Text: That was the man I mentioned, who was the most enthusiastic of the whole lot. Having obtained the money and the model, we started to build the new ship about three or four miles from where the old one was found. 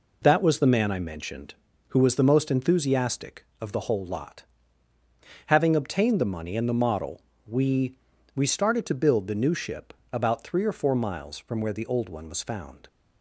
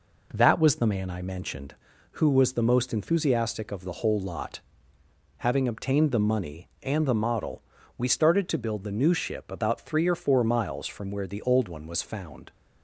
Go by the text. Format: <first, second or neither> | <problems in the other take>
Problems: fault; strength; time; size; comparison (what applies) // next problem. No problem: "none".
second | says "we" twice; at 8.3 s // pauses between "ship" and "about"; slight; at 9.9 s; 0.20 s long